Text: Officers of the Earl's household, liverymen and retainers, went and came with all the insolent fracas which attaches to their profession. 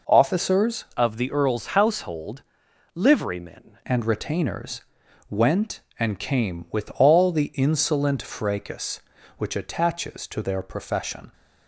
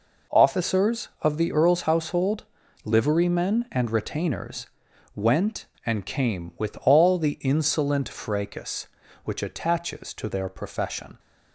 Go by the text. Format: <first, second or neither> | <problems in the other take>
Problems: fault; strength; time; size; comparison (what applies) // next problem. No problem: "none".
second | changes voice from "of" to "liverymen"; from 0.9 to 3.7 s; 2.8 s long